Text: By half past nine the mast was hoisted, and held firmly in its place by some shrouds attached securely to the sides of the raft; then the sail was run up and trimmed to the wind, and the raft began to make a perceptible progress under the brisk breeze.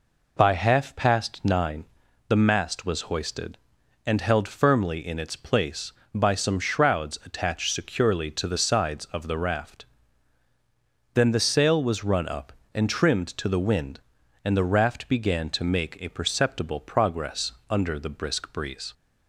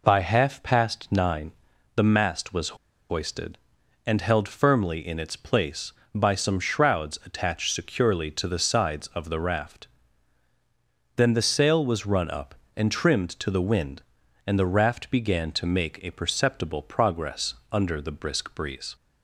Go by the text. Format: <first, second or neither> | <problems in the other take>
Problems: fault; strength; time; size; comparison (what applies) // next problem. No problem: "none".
first | pauses between "nine" and "the"; at 1.5 s; 0.44 s long; also in the first // pauses between "was" and "hoisted"; at 2.7 s; 0.36 s long // pauses between "progress" and "under"; slight; at 17.5 s; 0.16 s long; slight in the first